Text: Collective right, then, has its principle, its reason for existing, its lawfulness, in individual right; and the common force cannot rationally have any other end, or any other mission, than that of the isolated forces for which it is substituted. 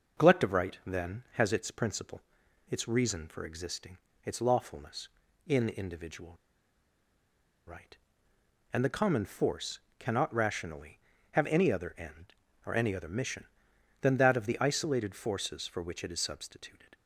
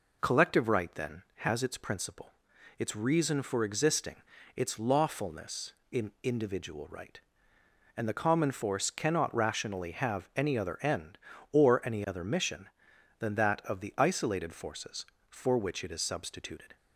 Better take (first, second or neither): second